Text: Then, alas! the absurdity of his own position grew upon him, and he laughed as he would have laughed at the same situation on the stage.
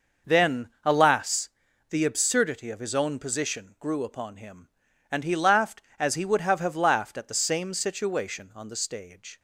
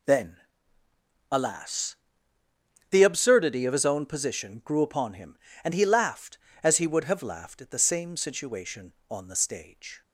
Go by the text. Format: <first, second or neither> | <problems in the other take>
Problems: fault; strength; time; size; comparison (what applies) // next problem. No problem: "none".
second | says "have" twice; at 6.6 s